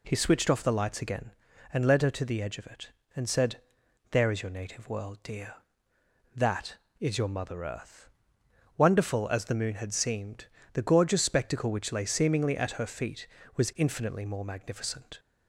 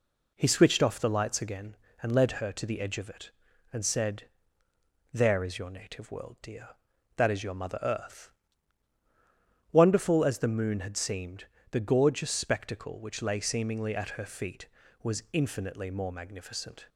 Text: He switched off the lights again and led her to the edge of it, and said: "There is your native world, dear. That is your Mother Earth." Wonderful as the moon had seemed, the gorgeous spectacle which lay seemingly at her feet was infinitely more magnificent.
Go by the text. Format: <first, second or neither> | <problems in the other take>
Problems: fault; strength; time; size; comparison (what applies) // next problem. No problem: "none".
neither | none